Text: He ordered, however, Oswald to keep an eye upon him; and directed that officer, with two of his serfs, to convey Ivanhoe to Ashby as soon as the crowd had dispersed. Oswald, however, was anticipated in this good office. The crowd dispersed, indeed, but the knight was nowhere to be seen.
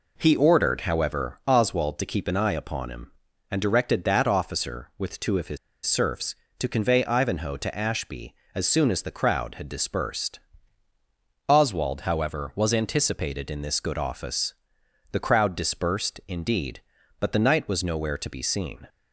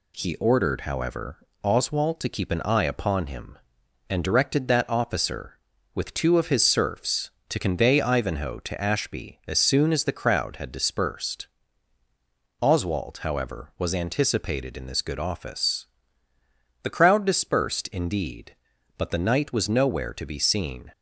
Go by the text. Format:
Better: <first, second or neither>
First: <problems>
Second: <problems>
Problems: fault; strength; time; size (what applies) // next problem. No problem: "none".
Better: second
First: pauses between "his" and "serfs"; slight; at 5.5 s; 0.28 s long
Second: none